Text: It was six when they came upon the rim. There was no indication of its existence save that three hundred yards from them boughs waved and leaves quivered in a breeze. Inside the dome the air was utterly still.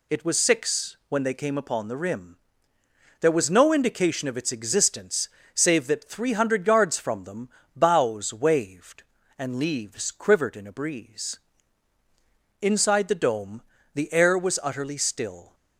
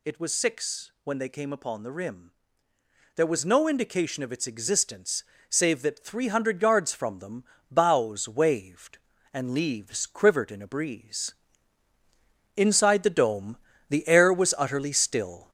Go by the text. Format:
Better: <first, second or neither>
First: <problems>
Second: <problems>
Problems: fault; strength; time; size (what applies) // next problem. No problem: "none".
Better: first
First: pauses between "existence" and "save"; slight; at 5.2 s; 0.26 s long // pauses between "them" and "boughs"; slight; at 7.4 s; 0.26 s long // pauses between "dome" and "the"; slight; at 13.6 s; 0.34 s long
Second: gets louder; noticeable; throughout; 4.5 dB // pauses between "existence" and "save"; slight; at 5.2 s; 0.26 s long // pauses between "them" and "boughs"; slight; at 7.4 s; 0.26 s long // pauses between "dome" and "the"; slight; at 13.5 s; 0.34 s long